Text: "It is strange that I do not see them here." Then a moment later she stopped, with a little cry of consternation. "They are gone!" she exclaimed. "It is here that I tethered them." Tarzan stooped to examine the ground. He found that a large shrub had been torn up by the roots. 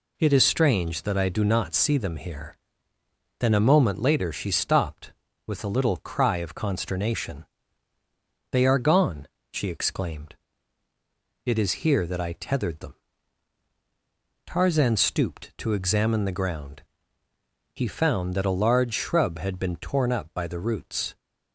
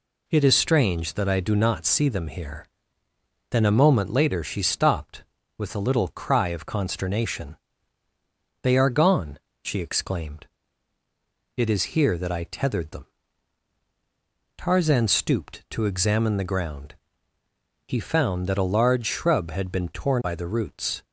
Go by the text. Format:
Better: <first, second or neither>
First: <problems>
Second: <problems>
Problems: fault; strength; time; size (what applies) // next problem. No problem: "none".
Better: first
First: none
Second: skips "up"; at 20.2 s